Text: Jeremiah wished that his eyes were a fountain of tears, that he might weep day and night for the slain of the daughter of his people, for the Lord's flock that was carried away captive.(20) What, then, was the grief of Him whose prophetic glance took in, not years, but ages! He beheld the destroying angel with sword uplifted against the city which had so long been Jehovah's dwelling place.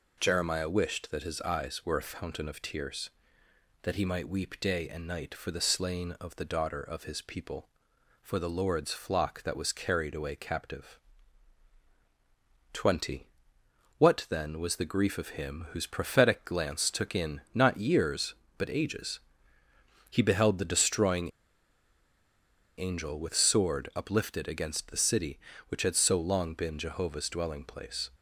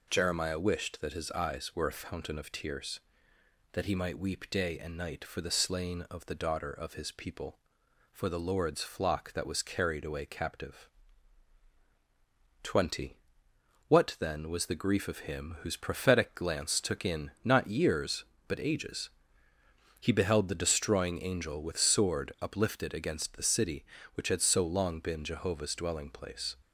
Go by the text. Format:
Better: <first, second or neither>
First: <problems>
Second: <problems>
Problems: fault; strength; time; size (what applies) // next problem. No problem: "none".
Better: second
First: pauses between "destroying" and "angel"; strong; at 21.3 s; 1.4 s long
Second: none